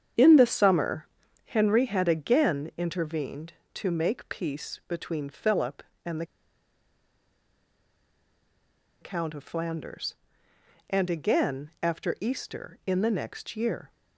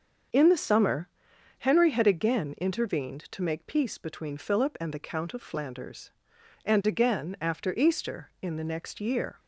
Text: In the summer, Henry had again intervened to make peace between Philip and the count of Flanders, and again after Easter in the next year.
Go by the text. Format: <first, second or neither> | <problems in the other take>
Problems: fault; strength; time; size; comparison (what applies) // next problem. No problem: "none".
second | starts louder than the rest; strong; until 1.5 s; 8.5 dB; also in the second // pauses between "the" and "count"; strong; at 6.2 s; 2.7 s long